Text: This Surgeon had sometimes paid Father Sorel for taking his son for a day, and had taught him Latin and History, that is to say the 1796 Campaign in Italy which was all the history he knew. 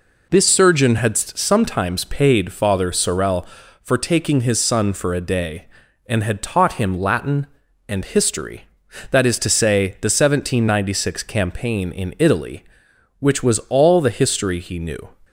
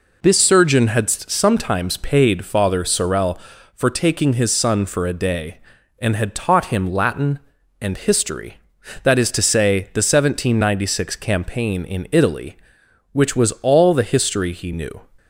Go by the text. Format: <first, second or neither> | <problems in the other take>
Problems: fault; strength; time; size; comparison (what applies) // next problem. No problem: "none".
neither | none